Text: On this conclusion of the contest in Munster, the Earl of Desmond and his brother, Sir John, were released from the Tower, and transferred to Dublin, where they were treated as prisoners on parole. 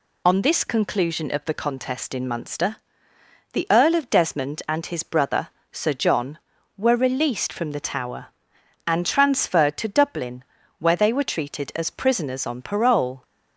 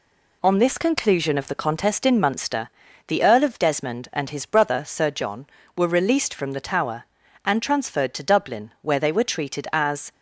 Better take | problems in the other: first | stops before "prisoners on parole"; at 10.1 s

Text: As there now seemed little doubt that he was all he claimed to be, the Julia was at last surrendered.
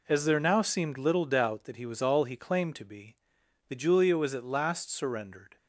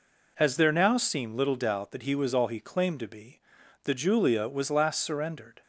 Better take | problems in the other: first | skips "at"; at 4.7 s

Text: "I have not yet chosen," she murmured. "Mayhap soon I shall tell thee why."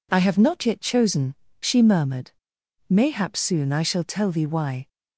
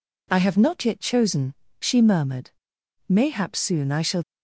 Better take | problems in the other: first | stops before "tell thee why"; at 4.2 s

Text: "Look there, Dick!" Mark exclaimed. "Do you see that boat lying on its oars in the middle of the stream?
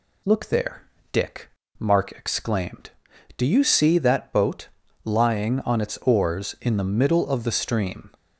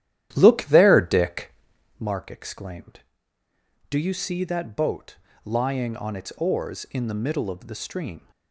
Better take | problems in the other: first | starts louder than the rest; strong; until 2.1 s; 11.5 dB // pauses between "boat" and "lying"; slight; at 5.1 s; 0.26 s long; slight in the first

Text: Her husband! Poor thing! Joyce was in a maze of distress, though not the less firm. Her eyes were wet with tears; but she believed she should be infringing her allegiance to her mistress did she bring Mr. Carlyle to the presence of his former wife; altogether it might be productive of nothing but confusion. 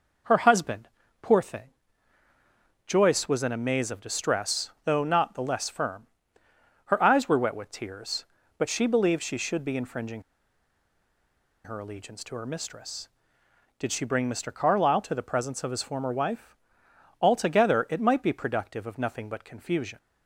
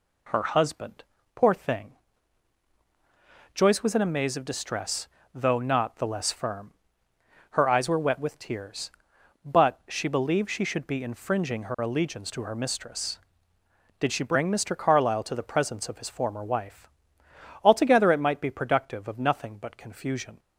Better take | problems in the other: second | pauses between "infringing" and "her"; strong; at 10.2 s; 1.4 s long

